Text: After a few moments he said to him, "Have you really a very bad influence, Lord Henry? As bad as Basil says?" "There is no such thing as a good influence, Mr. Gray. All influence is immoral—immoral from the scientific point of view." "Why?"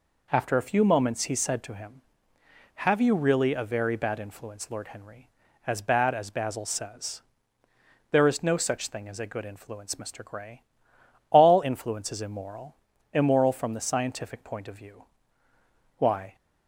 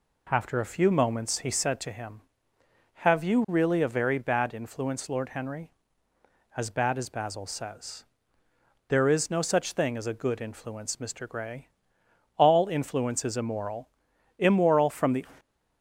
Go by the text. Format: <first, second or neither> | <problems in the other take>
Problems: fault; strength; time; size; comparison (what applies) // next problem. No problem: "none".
first | stops before "scientific point of view Why"; at 15.3 s